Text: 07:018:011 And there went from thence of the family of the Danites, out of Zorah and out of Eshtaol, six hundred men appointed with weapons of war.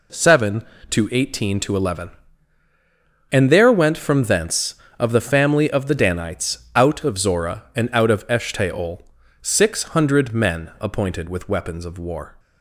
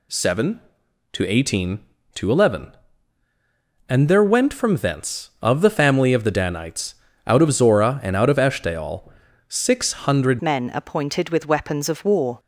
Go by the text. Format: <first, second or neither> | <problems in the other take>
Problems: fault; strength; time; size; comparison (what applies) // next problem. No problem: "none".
first | changes voice at "men"; from 10.4 s on; 1.9 s long